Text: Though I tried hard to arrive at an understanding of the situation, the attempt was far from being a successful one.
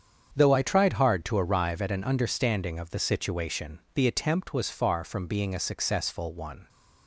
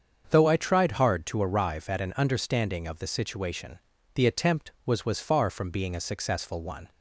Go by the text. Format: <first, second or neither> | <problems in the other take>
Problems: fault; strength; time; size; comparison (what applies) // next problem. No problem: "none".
first | starts louder than the rest; until 1.3 s; 7 dB; strong in the first // says "was" twice; at 5.0 s